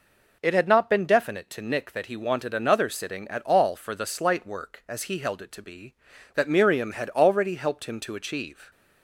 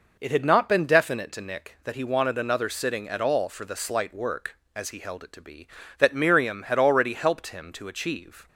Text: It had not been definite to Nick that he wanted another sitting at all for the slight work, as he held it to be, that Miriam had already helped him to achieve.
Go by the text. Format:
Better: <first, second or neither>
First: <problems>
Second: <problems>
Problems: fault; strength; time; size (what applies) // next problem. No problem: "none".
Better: neither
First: none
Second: none